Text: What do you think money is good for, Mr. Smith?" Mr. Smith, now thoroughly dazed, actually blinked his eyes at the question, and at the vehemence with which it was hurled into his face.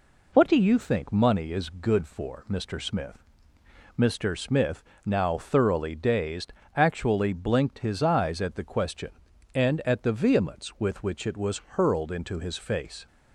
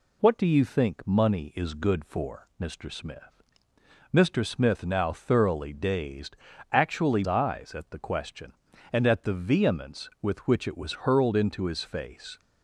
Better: first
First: none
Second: skips "blinked his"; at 7.2 s

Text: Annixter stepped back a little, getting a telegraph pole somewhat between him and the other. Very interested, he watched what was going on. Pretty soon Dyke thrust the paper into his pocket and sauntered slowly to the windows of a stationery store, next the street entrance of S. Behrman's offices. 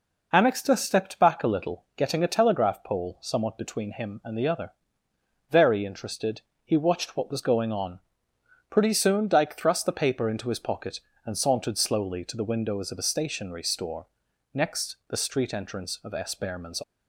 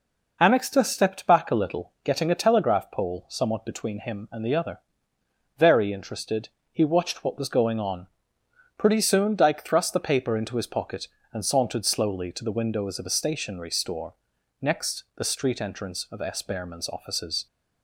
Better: second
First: stops before "offices"; at 16.8 s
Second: none

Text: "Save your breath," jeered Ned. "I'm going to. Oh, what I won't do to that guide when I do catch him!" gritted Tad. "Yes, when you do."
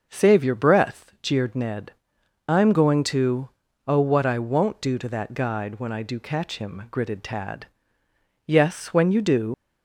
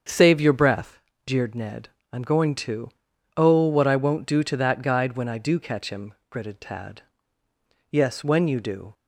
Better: second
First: starts louder than the rest; until 1.1 s; 6.5 dB // leaves "do" unfinished; at 9.5 s; 105 ms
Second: starts louder than the rest; until 1.3 s; 7 dB

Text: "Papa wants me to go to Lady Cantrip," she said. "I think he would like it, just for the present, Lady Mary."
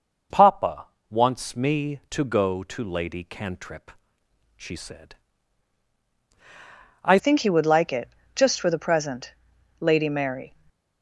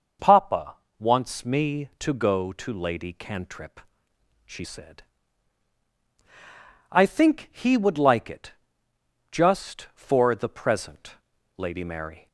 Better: second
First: pauses between "Papa" and "wants"; slight; at 0.8 s; 0.24 s long // changes voice at "think"; from 7.1 s on; 3.4 s long // stays silent after the last word; slight; from 10.4 s on; 0.6 s long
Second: pauses between "Papa" and "wants"; slight; at 0.7 s; 0.24 s long

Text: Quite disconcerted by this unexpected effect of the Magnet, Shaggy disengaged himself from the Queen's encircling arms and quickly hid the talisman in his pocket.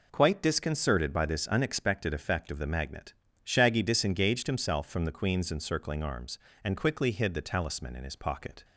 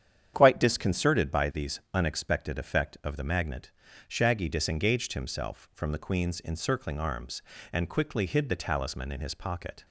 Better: first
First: none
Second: starts louder than the rest; strong; until 1.3 s; 9 dB // says "these" for "this"; at 1.5 s

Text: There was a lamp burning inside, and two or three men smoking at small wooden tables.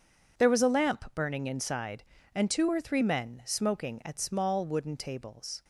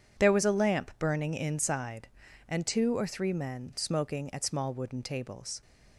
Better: neither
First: none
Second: none

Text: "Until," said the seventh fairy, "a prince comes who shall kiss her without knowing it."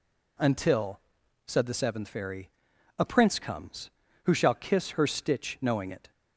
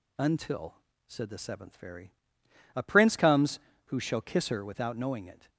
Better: second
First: says "stitch" for "without"; at 5.0 s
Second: none

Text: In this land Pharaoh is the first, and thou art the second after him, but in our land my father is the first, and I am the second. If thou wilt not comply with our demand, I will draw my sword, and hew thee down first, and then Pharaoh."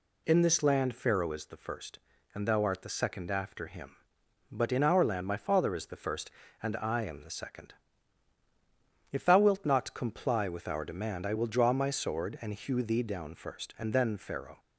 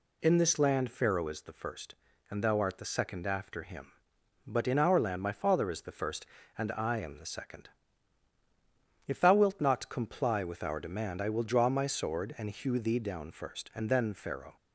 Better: neither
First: none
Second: none

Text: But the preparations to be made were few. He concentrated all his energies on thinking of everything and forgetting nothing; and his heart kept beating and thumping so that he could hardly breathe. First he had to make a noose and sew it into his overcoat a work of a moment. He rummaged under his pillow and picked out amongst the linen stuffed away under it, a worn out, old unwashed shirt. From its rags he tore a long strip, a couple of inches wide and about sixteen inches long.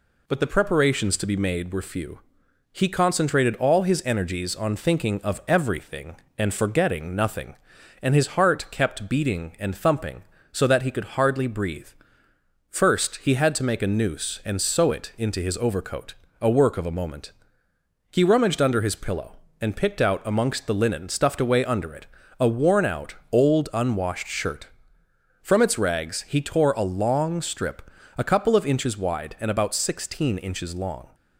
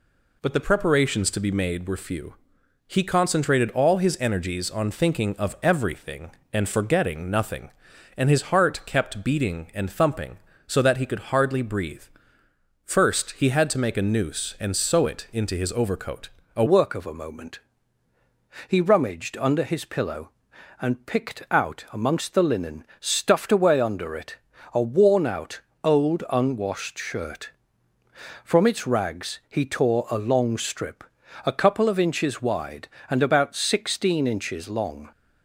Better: first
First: pauses between "overcoat" and "a"; slight; at 16.1 s; 0.26 s long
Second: pauses between "overcoat" and "a"; slight; at 16.2 s; 0.26 s long // changes voice at "work"; from 16.6 s on; 18.5 s long

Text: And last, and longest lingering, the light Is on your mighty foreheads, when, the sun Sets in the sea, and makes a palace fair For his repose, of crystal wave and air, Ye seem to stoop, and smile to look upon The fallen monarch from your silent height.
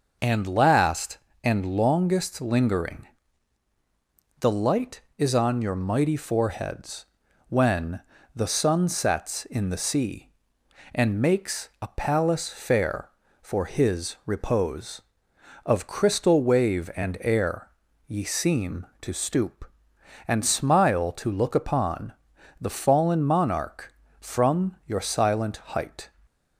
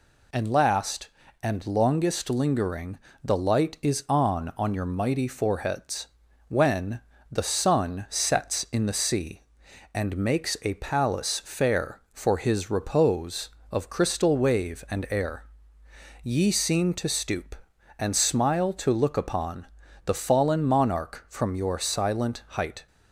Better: first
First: pauses between "upon" and "The"; noticeable; at 22.1 s; 0.48 s long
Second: says "on" twice; at 4.5 s // pauses between "upon" and "The"; at 19.6 s; 0.40 s long

